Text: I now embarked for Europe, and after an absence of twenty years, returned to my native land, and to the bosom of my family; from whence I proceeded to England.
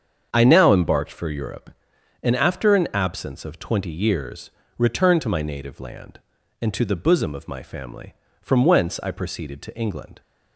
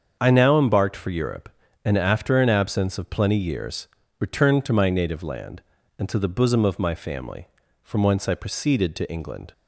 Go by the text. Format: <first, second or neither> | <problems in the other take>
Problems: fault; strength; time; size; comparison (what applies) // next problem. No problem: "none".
first | starts louder than the rest; until 1.2 s; 7 dB; strong in the first // says "plenty" for "twenty"; at 3.0 s